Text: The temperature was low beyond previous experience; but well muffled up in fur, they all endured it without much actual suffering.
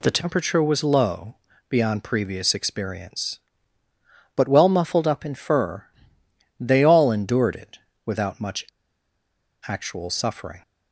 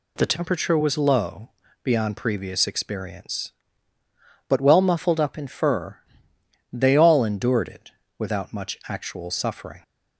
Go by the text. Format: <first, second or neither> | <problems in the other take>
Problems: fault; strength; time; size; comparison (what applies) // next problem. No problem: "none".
second | pauses between "low" and "beyond"; slight; at 1.3 s; 0.34 s long; slight in the second // pauses between "it" and "without"; slight; at 7.7 s; 0.26 s long; slight in the second // pauses between "much" and "actual"; at 8.6 s; 1.0 s long